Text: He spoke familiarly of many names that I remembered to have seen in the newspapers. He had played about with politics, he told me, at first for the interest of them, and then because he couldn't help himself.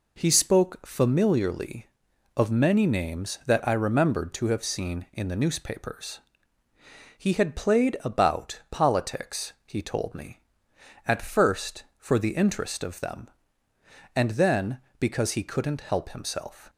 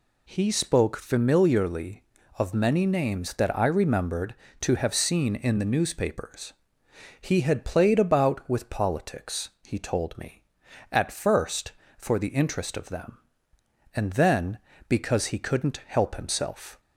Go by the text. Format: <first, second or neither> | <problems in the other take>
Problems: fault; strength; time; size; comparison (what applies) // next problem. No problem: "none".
second | skips "with"; at 8.6 s